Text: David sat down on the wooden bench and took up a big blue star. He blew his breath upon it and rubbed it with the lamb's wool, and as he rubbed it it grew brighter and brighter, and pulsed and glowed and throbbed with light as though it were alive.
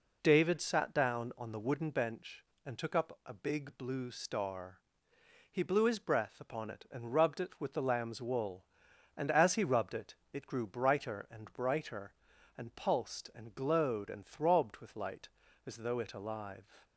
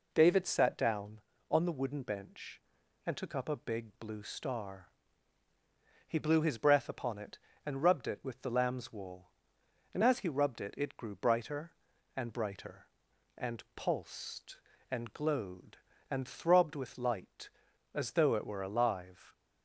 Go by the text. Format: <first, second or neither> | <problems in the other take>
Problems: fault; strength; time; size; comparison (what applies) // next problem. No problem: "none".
second | pauses between "it" and "it"; slight; at 10.1 s; 0.18 s long // skips "were"; at 16.1 s